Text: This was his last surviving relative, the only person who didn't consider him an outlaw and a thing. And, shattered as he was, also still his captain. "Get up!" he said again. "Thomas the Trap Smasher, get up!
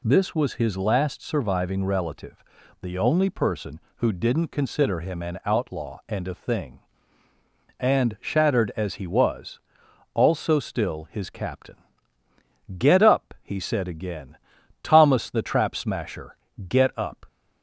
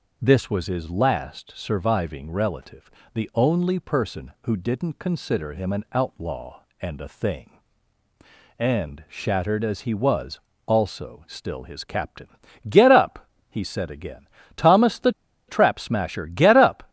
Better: first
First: none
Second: pauses between "the" and "Trap"; at 15.1 s; 0.37 s long

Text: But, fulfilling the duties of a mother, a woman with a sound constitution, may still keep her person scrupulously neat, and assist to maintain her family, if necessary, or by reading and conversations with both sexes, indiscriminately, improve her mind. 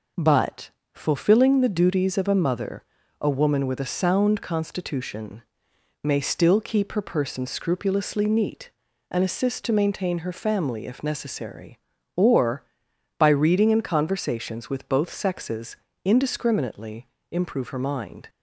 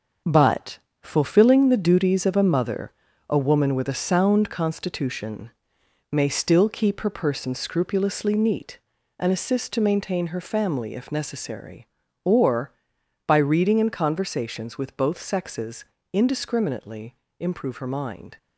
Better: first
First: none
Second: gets quieter; strong; throughout; 7.5 dB

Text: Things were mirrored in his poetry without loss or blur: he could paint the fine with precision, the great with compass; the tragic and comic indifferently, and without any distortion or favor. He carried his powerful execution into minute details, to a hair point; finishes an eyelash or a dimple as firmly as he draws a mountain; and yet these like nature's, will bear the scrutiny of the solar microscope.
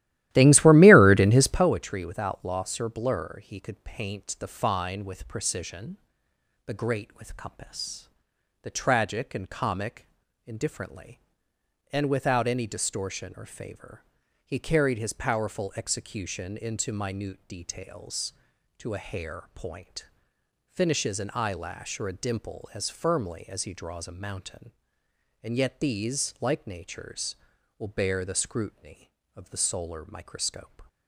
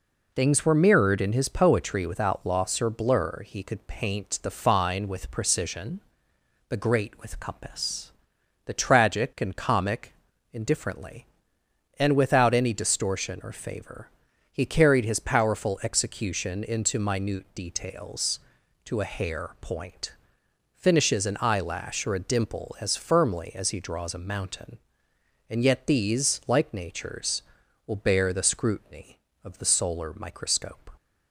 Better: second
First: starts louder than the rest; strong; until 1.7 s; 15 dB // pauses between "comic" and "indifferently"; at 10.0 s; 0.38 s long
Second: pauses between "comic" and "indifferently"; at 10.1 s; 0.38 s long

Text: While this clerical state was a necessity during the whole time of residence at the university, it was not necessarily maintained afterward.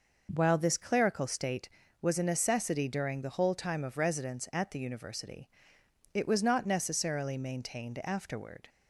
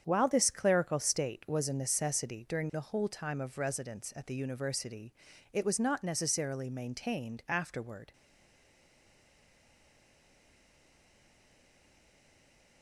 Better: first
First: none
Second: starts louder than the rest; strong; until 1.0 s; 8 dB // stays silent after the last word; strong; from 8.1 s on; 4.7 s long

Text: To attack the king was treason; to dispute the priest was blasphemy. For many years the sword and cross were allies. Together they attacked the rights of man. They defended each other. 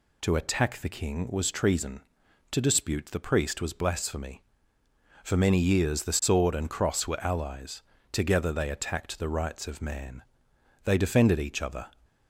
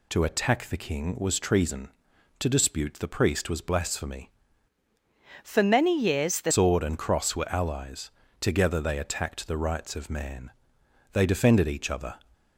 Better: first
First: none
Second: changes voice from "For" to "the"; from 5.4 to 6.5 s; 1.1 s long

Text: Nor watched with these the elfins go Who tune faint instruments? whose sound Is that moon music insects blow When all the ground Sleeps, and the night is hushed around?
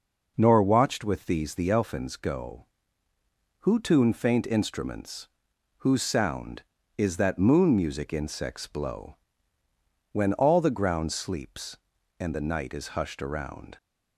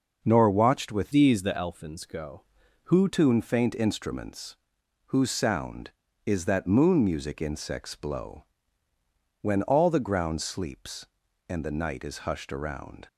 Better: first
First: pauses between "blow" and "When"; noticeable; at 9.1 s; 0.95 s long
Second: changes voice from "these" to "Who"; from 1.1 to 3.0 s; 1.9 s long // pauses between "blow" and "When"; noticeable; at 8.4 s; 0.96 s long

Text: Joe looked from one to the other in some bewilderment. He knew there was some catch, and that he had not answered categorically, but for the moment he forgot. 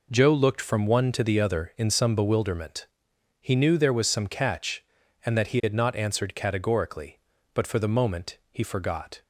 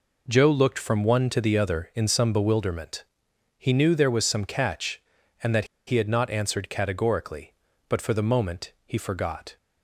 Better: first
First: none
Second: pauses between "that" and "he"; slight; at 5.6 s; 0.22 s long

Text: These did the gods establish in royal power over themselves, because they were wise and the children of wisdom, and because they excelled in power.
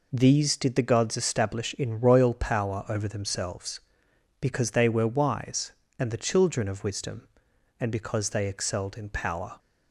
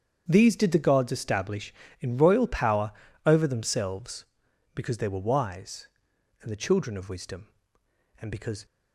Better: first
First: none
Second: starts louder than the rest; strong; until 1.2 s; 7.5 dB // pauses between "power" and "over"; slight; at 2.9 s; 0.34 s long // stops before "they excelled in power"; at 8.6 s

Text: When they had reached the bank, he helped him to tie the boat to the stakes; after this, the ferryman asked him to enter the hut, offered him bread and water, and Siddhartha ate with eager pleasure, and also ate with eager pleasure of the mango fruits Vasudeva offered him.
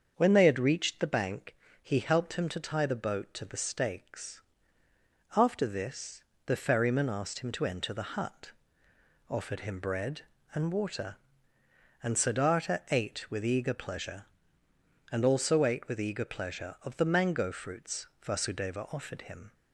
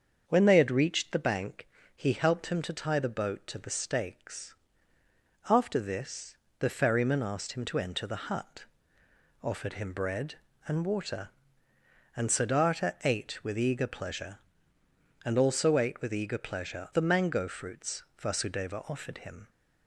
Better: first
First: starts louder than the rest; until 1.1 s; 7 dB // pauses between "fruits" and "Vasudeva"; slight; at 18.0 s; 0.16 s long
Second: starts louder than the rest; until 1.2 s; 7 dB // skips "of"; at 16.9 s // pauses between "fruits" and "Vasudeva"; slight; at 18.0 s; 0.16 s long

